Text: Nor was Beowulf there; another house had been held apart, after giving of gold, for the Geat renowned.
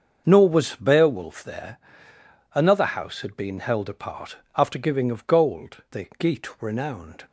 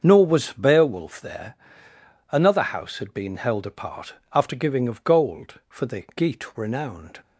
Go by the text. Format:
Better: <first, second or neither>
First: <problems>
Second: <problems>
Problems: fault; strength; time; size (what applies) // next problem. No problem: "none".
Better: second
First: starts louder than the rest; until 1.2 s; 6.5 dB // skips "for"; at 5.8 s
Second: starts louder than the rest; until 1.0 s; 7 dB